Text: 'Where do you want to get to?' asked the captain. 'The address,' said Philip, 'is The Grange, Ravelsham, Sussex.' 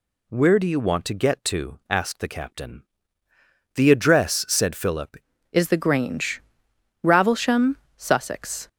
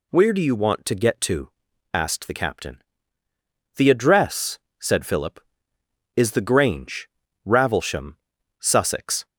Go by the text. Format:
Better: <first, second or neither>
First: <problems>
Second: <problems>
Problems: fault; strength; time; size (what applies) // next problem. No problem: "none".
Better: second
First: changes voice at "is"; from 5.5 s on; 3.1 s long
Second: none